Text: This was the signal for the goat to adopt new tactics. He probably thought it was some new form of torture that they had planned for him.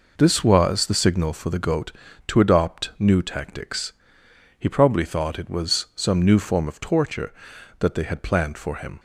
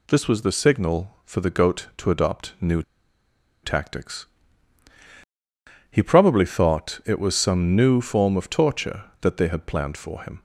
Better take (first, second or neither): first